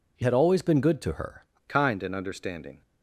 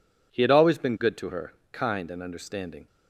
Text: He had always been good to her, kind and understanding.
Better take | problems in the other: second | changes voice from "had" to "her"; from 0.2 to 1.4 s; 1.2 s long

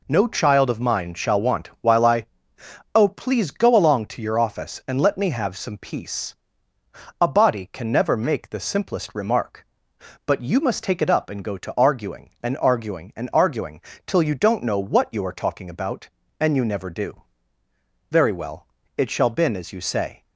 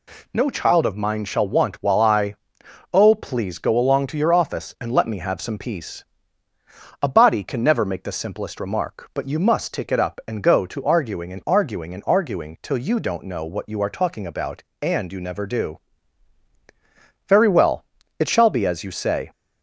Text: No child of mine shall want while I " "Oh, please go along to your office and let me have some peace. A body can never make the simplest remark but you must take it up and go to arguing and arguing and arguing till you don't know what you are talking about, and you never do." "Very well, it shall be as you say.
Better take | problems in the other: second | pauses between "arguing" and "till"; slight; at 13.7 s; 0.26 s long // says "been" for "be"; at 19.2 s

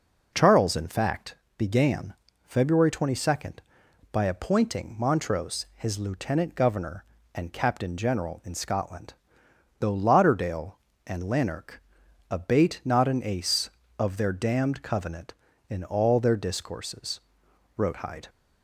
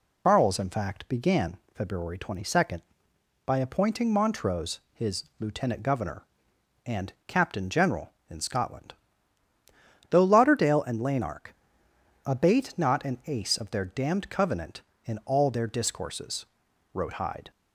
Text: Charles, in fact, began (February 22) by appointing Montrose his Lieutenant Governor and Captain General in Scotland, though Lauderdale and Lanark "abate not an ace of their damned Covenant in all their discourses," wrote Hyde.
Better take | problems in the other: first | loses the start of "Charles"; at 0.2 s; 110 ms // pauses between "his" and "Lieutenant"; slight; at 5.2 s; 0.16 s long // pauses between "Lanark" and "abate"; noticeable; at 11.5 s; 0.70 s long; noticeable in the first

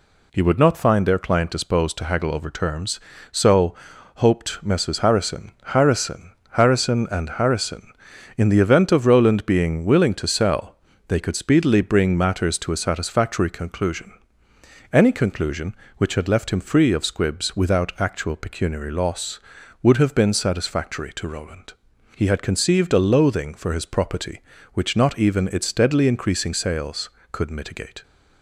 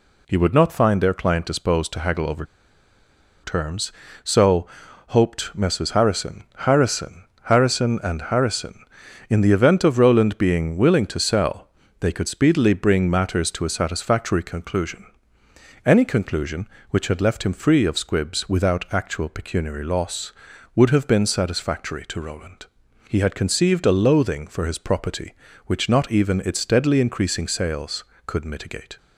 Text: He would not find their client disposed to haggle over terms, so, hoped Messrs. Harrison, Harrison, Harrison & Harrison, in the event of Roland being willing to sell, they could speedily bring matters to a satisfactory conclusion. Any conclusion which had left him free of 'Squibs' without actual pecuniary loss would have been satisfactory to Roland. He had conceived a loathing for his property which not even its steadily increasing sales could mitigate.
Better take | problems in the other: first | pauses between "over" and "terms"; at 2.4 s; 0.99 s long

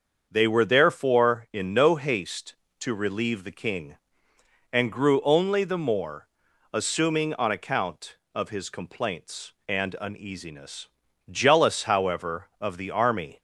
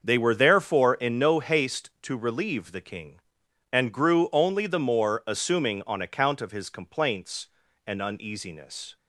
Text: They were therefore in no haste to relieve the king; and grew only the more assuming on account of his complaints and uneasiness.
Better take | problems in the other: second | starts louder than the rest; until 1.3 s; 7 dB; also in the second // pauses between "more" and "assuming"; noticeable; at 6.2 s; 0.46 s long // goes on to say "Jealous however of the army"; strong; from 11.2 s on; 2.1 s long

